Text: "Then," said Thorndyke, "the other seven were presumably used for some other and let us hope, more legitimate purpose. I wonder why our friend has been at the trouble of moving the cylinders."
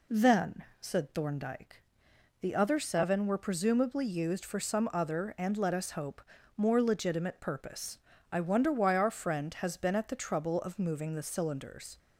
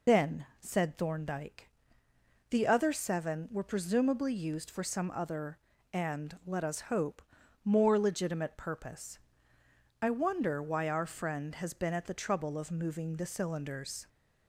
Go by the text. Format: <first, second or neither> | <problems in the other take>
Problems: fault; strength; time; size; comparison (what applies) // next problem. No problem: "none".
first | loses the start of "Then"; at 0.0 s; 125 ms